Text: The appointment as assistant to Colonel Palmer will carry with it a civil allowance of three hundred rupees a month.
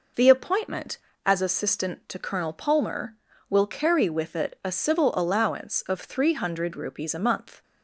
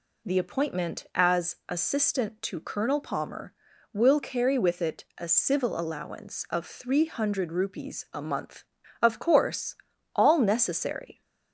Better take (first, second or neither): first